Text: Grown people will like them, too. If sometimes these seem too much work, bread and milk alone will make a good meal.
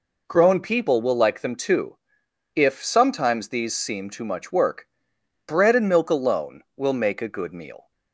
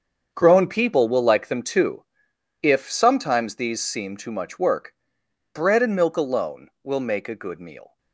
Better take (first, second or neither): first